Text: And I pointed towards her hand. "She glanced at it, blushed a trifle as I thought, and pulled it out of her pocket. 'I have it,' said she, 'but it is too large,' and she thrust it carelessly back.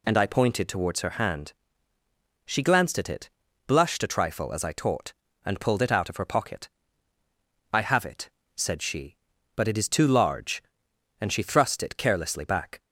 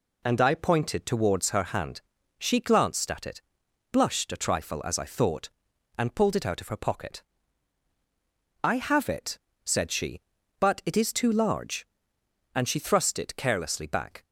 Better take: second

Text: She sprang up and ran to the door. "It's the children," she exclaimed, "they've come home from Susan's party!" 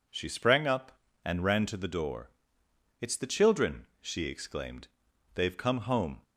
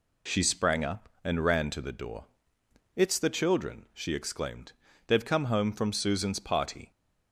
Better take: second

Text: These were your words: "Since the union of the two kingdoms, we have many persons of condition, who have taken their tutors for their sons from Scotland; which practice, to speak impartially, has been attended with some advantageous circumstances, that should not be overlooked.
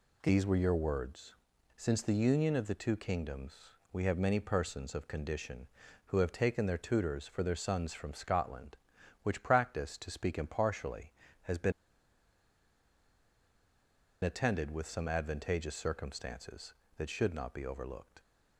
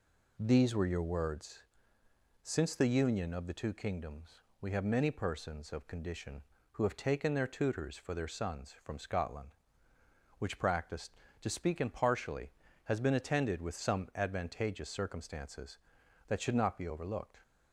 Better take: second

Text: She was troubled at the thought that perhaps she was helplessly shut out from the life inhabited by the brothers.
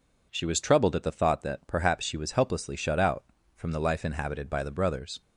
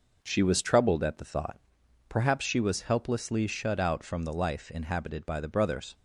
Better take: first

